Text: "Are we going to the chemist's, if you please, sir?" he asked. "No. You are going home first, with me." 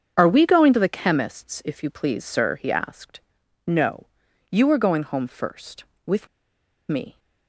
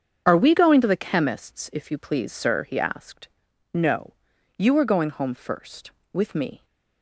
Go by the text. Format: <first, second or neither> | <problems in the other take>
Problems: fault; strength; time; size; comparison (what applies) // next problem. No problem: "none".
second | starts louder than the rest; strong; until 1.1 s; 7.5 dB; strong in the second // pauses between "with" and "me"; noticeable; at 6.2 s; 0.61 s long